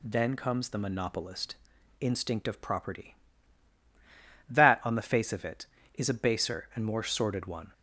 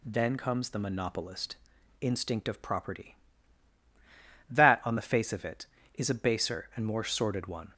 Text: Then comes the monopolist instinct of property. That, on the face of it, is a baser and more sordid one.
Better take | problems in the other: neither | pauses between "monopolist" and "instinct"; noticeable; the same in both

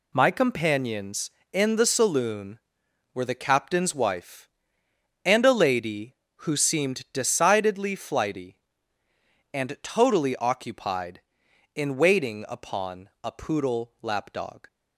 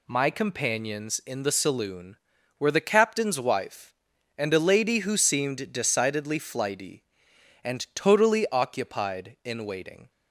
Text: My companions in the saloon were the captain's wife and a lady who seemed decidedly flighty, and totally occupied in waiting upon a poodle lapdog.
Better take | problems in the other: first | stops before "upon a poodle lapdog"; at 10.0 s

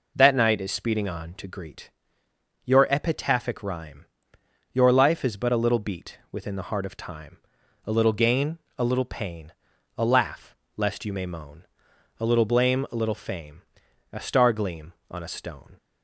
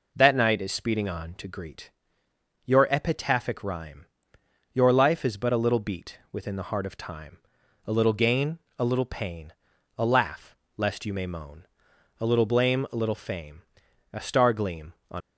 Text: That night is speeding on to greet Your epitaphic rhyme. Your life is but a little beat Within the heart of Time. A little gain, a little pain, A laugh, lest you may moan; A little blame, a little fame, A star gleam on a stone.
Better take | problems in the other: first | pauses between "greet" and "Your"; noticeable; at 1.8 s; 0.76 s long; noticeable in the first // stops before "a stone"; at 15.2 s

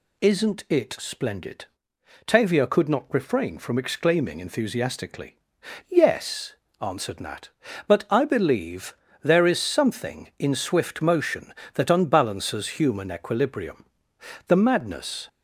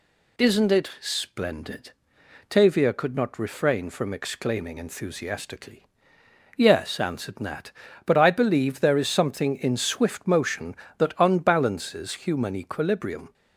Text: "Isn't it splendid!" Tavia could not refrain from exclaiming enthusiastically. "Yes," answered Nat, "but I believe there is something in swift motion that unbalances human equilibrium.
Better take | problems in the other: second | pauses between "believe" and "there"; slight; at 8.9 s; 0.26 s long // goes on to say "The madness"; noticeable; from 14.4 s on; 0.80 s long

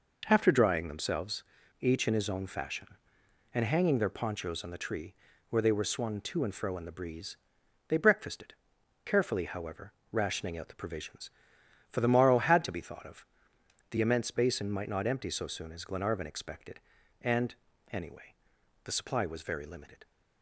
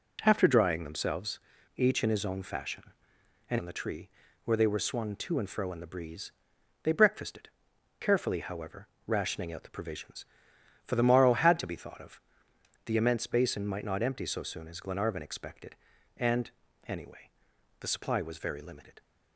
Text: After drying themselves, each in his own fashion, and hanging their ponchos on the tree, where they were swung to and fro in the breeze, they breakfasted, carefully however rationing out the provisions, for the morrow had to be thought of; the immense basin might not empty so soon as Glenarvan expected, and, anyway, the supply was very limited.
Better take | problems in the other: first | skips "hanging their ponchos"; at 3.5 s // pauses between "however" and "rationing"; slight; at 8.8 s; 0.20 s long; slight in the first

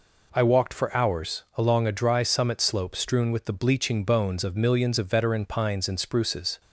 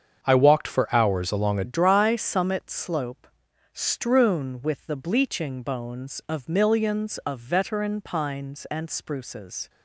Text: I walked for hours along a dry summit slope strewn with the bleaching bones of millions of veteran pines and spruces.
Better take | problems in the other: first | starts louder than the rest; strong; until 1.2 s; 7.5 dB // changes voice at "dry"; from 1.6 s on; 8.0 s long // pauses between "slope" and "strewn"; noticeable; at 3.2 s; 0.46 s long

